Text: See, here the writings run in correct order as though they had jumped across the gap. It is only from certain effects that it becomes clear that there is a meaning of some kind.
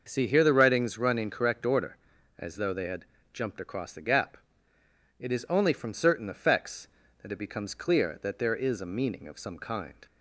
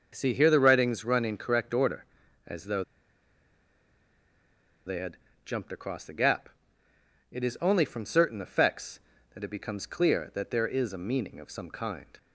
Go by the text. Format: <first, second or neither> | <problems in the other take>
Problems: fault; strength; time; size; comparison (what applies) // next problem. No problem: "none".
first | starts louder than the rest; noticeable; until 1.1 s; 6 dB; noticeable in the first // pauses between "though" and "they"; strong; at 2.8 s; 2.0 s long // pauses between "had" and "jumped"; slight; at 5.1 s; 0.26 s long; slight in the first